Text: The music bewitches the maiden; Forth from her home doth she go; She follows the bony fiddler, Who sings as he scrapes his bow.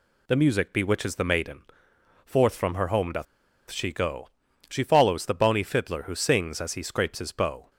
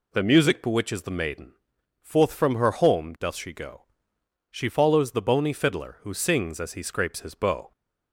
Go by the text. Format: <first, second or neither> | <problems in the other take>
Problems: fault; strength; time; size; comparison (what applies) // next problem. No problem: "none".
second | pauses between "doth" and "she"; at 3.2 s; 0.44 s long